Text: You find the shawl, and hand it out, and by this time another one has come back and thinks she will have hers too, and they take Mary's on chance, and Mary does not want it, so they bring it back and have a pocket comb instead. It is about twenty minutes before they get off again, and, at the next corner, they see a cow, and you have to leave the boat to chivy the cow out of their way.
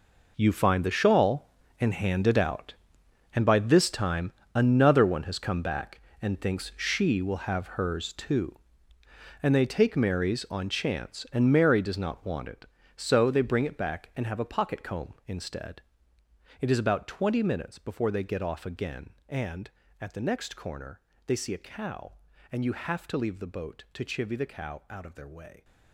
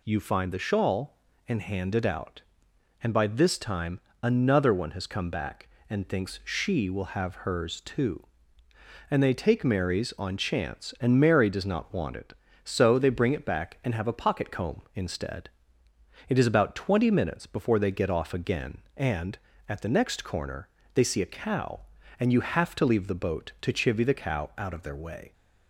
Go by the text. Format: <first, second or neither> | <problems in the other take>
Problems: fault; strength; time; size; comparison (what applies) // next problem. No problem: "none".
second | gets quieter; strong; throughout; 13.5 dB // pauses between "time" and "another"; slight; at 4.3 s; 0.22 s long; slight in the second